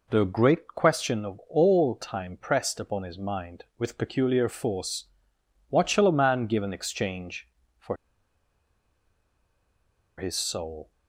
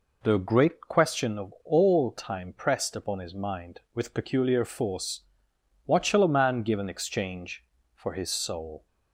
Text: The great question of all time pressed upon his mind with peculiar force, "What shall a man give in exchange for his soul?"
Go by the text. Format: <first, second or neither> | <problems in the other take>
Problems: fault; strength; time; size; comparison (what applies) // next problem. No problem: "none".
second | pauses between "for" and "his"; strong; at 7.9 s; 2.2 s long